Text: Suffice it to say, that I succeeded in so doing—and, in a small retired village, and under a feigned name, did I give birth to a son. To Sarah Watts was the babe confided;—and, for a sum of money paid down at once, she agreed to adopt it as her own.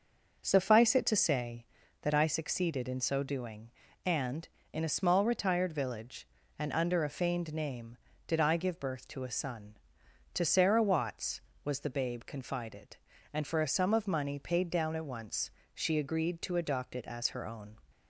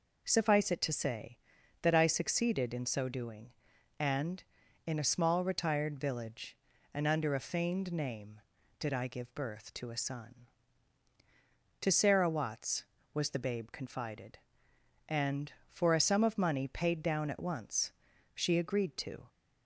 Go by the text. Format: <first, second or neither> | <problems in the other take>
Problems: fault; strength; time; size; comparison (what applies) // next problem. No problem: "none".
first | stops before "adopt it as her own"; at 19.2 s